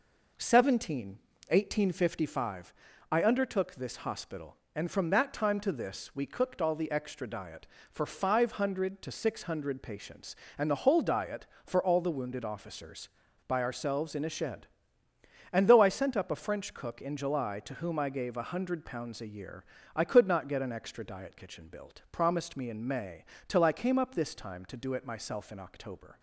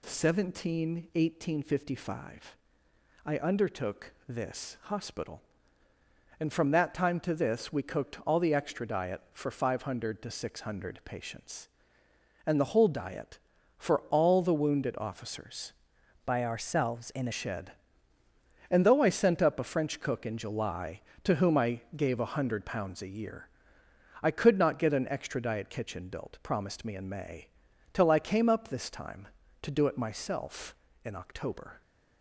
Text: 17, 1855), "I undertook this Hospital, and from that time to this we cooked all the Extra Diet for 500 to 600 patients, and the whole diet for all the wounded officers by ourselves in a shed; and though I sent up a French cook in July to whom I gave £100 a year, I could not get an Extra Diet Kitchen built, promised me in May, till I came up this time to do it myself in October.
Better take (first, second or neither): first